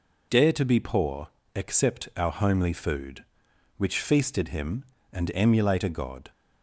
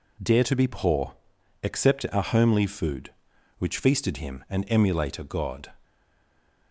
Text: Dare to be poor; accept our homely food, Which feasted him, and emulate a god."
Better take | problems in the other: first | stays silent after the last word; slight; from 5.8 s on; 0.9 s long

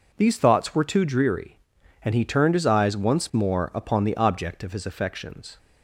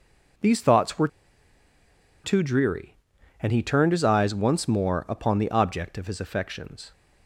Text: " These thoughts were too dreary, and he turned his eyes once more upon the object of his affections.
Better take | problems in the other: first | pauses between "were" and "too"; at 1.0 s; 1.1 s long

